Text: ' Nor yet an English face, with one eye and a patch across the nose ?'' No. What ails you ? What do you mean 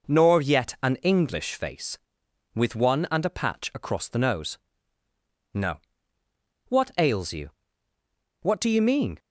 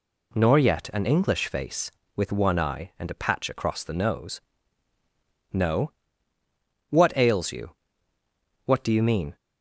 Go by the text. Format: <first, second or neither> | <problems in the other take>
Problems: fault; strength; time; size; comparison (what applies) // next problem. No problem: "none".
second | skips "eye"; at 3.0 s